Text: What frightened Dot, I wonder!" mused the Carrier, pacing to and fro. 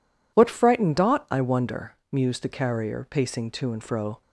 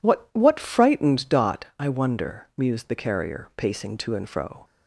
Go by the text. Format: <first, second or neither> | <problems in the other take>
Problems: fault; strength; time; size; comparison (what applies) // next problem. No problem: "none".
first | says "What" twice; at 0.3 s